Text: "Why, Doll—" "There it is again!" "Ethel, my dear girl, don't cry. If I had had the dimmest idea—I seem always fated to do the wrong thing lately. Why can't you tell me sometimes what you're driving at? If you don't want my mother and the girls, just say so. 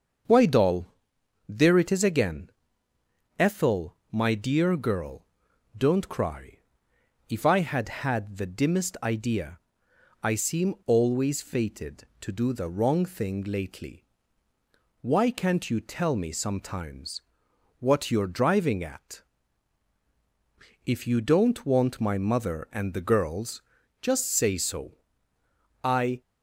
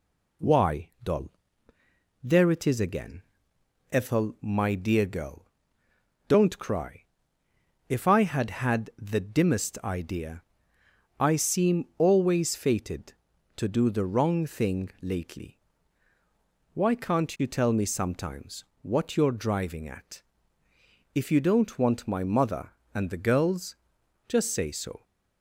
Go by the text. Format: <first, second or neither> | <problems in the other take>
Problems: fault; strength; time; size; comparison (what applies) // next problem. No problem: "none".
second | starts louder than the rest; until 1.8 s; 6.5 dB // pauses between "sometimes" and "what"; noticeable; at 17.2 s; 0.56 s long; slight in the second // goes on to say "I"; slight; from 25.8 s on; 0.38 s long